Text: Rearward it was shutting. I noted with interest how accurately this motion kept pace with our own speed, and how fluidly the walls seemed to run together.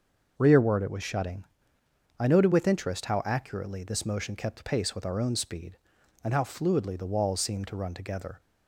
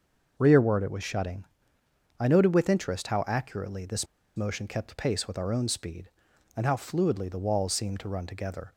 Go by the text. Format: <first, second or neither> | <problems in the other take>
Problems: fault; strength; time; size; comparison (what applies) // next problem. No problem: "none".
first | starts louder than the rest; noticeable; until 1.3 s; 6 dB // pauses between "this" and "motion"; slight; at 4.0 s; 0.30 s long